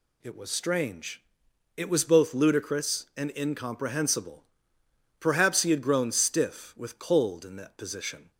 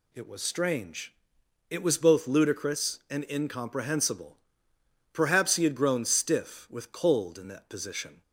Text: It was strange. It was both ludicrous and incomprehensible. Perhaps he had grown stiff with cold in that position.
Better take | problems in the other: neither | none

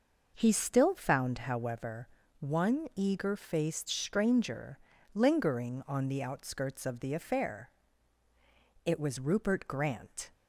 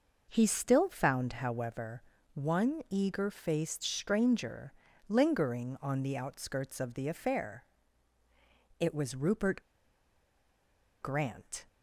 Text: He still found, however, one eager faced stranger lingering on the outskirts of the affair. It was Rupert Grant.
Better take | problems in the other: first | pauses between "stranger" and "lingering"; slight; at 4.7 s; 0.36 s long; slight in the first // pauses between "Rupert" and "Grant"; strong; at 9.6 s; 1.3 s long

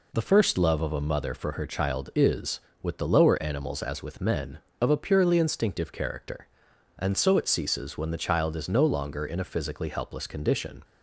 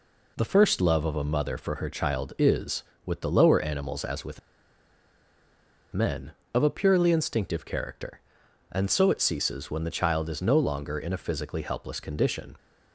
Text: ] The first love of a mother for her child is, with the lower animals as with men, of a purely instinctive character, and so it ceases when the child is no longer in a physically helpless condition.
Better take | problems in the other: first | pauses between "with" and "men"; strong; at 4.4 s; 1.5 s long

